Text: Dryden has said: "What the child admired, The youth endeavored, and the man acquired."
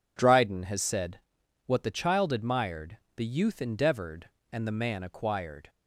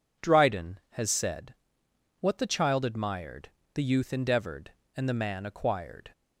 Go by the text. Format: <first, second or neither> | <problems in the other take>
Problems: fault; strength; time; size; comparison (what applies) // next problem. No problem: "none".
neither | none